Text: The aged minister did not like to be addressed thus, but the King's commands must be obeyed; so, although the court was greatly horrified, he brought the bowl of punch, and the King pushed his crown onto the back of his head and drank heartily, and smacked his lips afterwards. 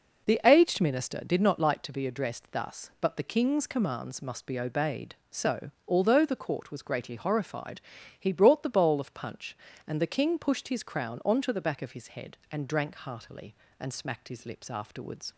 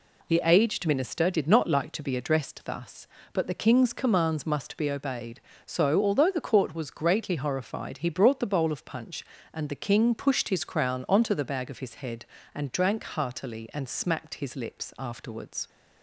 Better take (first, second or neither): first